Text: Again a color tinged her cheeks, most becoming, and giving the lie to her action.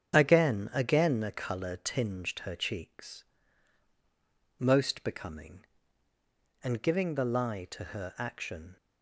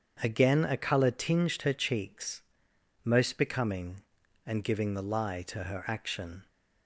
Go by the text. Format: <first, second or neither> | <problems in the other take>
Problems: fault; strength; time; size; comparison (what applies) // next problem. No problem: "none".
second | starts louder than the rest; strong; until 1.1 s; 8 dB; strong in the second // says "Again" twice; at 0.7 s